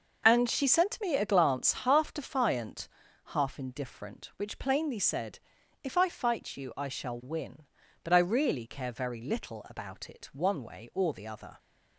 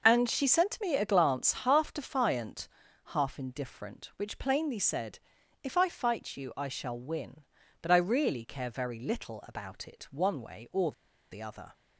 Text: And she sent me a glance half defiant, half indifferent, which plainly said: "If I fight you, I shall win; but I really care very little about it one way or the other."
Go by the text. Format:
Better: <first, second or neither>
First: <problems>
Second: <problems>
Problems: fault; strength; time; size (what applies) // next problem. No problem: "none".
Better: first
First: none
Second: pauses between "or" and "the"; at 10.9 s; 0.39 s long